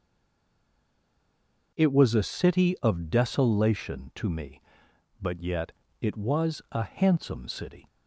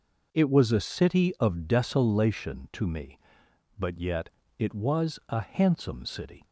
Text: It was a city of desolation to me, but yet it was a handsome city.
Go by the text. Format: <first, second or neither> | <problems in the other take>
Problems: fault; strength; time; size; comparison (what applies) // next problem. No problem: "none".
second | stays silent before the first word; noticeable; until 1.7 s; 1.7 s long // pauses between "yet" and "it"; slight; at 5.7 s; 0.32 s long; slight in the second